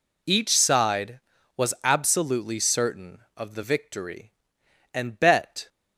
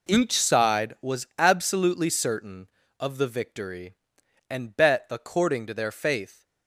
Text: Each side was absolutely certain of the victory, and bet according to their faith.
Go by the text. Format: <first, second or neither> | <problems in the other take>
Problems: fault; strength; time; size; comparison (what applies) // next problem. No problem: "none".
second | stops before "according to their faith"; at 5.6 s